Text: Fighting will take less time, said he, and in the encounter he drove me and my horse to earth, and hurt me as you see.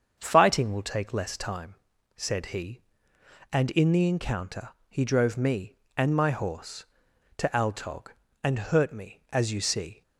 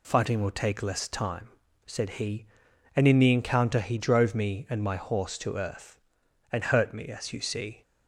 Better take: second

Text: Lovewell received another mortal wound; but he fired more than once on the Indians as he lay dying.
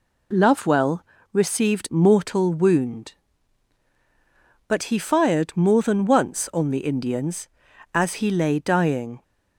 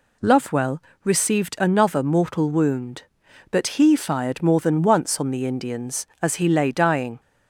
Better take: second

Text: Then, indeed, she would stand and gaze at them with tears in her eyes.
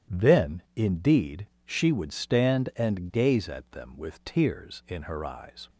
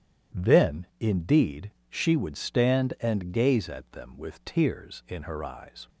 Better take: neither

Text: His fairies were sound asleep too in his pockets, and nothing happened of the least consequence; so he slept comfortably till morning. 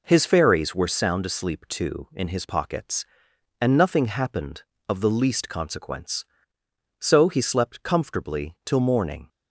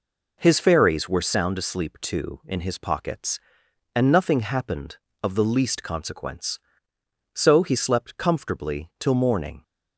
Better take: neither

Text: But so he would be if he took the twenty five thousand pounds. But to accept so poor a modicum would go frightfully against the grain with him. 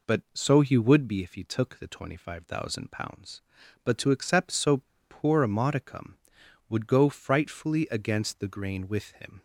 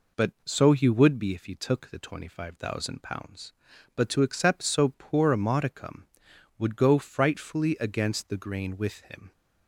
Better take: second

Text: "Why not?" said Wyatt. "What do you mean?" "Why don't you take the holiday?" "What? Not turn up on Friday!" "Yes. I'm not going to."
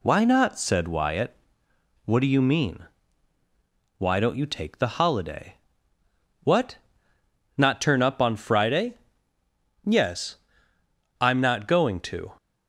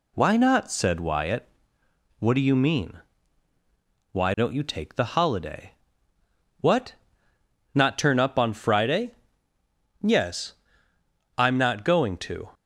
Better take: neither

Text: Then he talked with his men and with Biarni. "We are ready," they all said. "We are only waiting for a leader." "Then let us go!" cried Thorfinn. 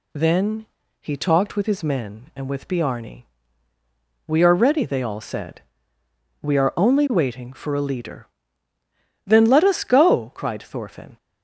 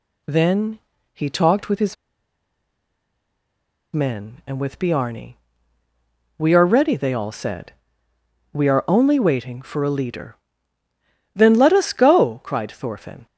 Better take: first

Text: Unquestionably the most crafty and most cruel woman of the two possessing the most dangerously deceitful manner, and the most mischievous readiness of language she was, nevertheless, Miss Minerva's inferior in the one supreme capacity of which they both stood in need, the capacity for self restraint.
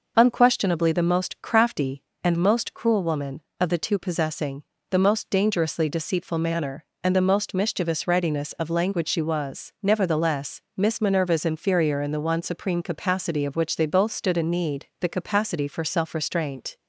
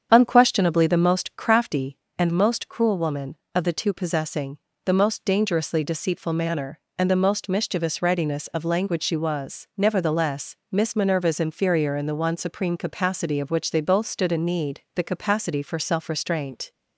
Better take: first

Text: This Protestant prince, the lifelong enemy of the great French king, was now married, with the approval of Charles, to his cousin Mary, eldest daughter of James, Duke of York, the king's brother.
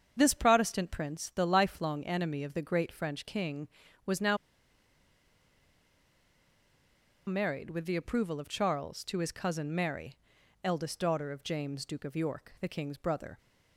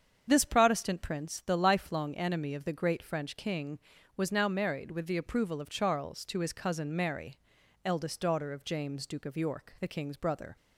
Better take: second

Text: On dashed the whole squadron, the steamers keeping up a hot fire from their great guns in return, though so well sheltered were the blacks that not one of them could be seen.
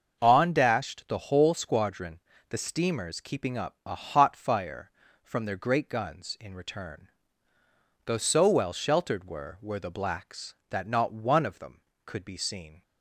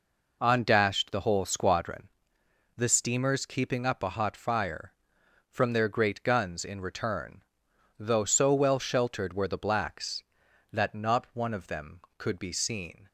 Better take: second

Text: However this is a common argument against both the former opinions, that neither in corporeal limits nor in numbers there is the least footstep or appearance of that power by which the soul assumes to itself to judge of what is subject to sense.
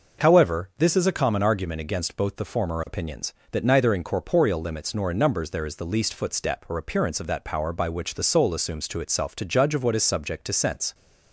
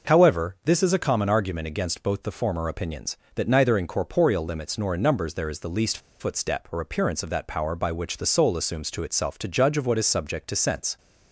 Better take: first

